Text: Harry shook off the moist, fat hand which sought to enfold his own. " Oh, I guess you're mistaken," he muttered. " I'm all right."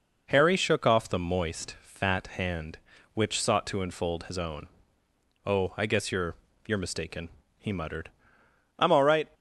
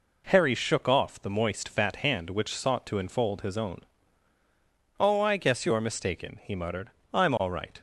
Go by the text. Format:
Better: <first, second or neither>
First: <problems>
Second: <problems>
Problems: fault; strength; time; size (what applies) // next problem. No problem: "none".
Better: second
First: says "you're" twice; at 6.6 s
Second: none